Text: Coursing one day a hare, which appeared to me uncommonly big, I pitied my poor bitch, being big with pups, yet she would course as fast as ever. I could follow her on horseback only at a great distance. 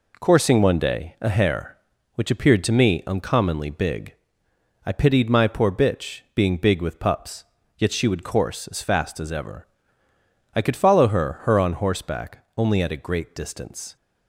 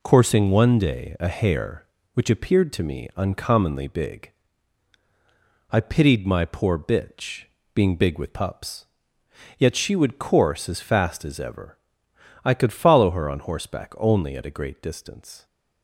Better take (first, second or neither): second